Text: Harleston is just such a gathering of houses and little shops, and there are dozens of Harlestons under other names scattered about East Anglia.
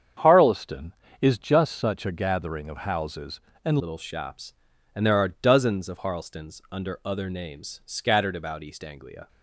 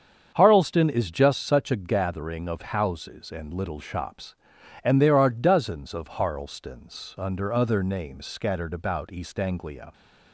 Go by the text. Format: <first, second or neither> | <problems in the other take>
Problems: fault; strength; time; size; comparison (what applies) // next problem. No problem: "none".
second | starts louder than the rest; strong; until 1.4 s; 8 dB; strong in the second // changes voice at "little"; from 3.7 s on; 5.5 s long